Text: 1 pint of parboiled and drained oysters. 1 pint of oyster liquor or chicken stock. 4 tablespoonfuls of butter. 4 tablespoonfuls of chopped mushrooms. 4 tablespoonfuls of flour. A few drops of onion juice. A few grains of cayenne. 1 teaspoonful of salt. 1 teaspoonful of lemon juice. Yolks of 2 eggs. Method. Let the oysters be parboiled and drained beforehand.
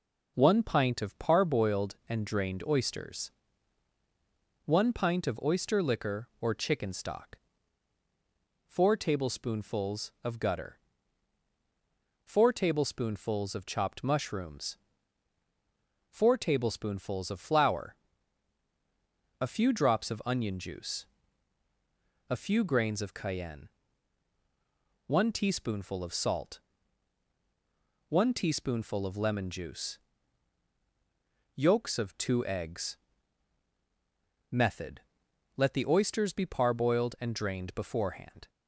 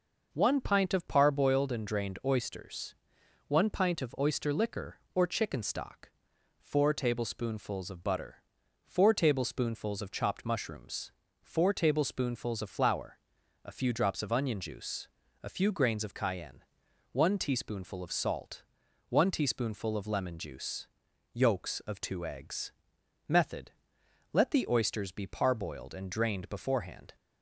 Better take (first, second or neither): second